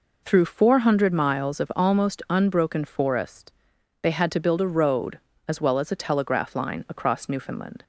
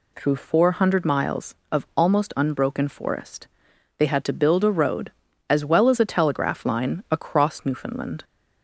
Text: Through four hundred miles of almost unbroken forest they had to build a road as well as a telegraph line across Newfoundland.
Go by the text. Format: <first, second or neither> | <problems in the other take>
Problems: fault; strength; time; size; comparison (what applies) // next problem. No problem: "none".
neither | pauses between "forest" and "they"; noticeable; the same in both